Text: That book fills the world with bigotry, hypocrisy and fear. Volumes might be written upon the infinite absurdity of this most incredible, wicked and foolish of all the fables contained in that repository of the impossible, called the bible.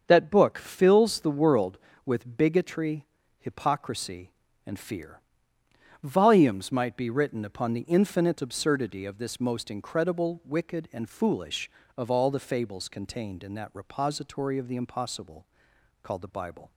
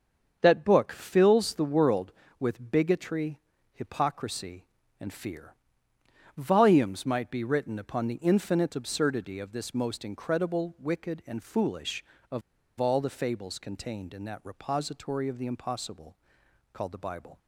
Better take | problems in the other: first | starts louder than the rest; until 1.4 s; 7 dB; also in the first // pauses between "of" and "all"; at 12.4 s; 0.38 s long

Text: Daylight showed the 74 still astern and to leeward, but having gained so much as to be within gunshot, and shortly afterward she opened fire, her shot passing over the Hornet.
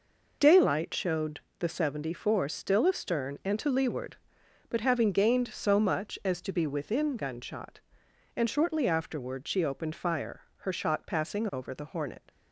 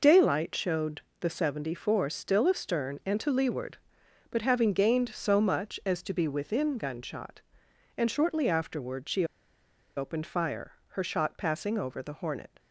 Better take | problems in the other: first | pauses between "showed" and "the"; slight; at 1.0 s; 0.20 s long; slight in the first // pauses between "she" and "opened"; noticeable; at 9.2 s; 0.72 s long

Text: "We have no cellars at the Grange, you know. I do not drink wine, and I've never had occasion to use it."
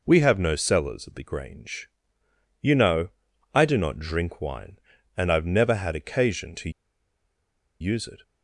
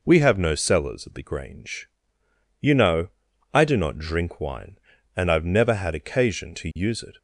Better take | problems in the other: second | pauses between "to" and "use"; at 6.7 s; 1.1 s long

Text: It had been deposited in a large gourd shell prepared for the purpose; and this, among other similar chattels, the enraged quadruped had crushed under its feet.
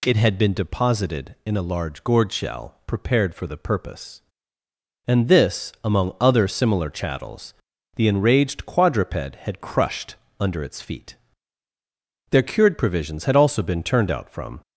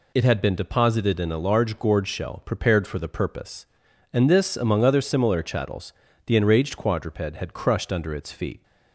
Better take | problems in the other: second | pauses between "crushed" and "under"; slight; at 10.1 s; 0.22 s long // goes on to say "Their cured provisions had also been turned out from"; strong; from 12.3 s on; 2.3 s long

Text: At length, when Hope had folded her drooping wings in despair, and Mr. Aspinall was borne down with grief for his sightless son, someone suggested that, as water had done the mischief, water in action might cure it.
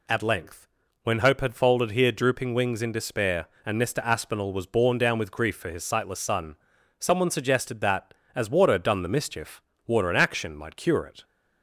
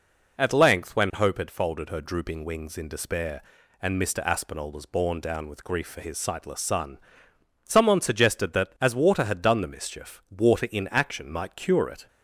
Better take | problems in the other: second | says "here" for "her"; at 1.9 s

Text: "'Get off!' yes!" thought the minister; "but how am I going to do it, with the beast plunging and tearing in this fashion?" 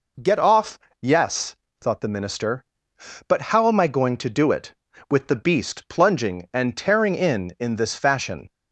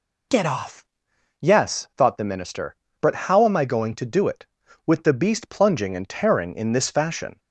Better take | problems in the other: second | says "in" twice; at 7.5 s

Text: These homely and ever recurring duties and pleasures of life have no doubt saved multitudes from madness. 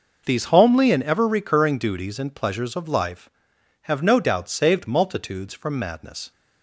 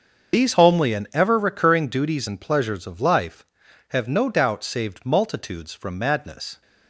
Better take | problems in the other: first | loses the start of "These"; at 0.3 s; 30 ms // starts louder than the rest; until 1.4 s; 6.5 dB

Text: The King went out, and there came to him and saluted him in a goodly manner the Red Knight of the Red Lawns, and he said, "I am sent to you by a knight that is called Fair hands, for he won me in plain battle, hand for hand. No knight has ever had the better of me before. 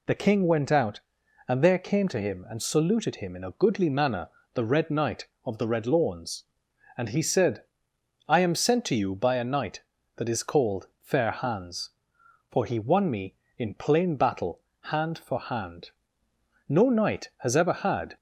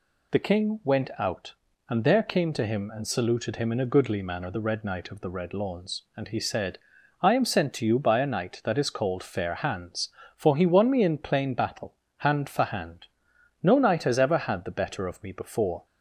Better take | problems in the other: second | pauses between "manner" and "the"; slight; at 4.2 s; 0.26 s long // stops before "the better of me before"; at 18.1 s

